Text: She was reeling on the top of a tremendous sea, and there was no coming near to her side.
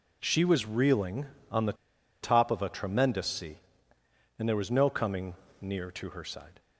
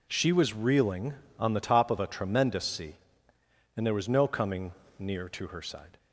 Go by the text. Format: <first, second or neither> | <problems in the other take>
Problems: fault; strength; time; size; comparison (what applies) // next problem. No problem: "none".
second | pauses between "the" and "top"; noticeable; at 1.7 s; 0.49 s long // pauses between "coming" and "near"; slight; at 5.3 s; 0.28 s long; slight in the second